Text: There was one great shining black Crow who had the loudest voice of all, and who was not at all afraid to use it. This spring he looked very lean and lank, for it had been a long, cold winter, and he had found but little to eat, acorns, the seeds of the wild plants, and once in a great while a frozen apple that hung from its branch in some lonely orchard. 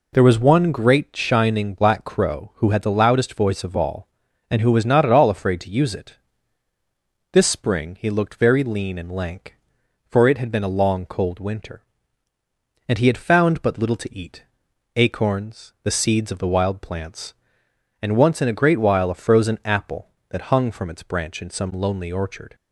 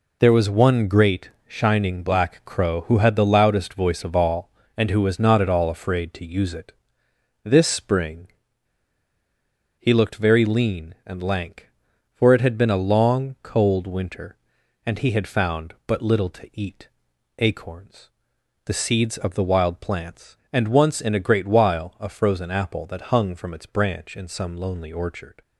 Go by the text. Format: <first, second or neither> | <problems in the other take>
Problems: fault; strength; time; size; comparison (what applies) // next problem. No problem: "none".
first | pauses between "spring" and "he"; strong; at 8.2 s; 1.5 s long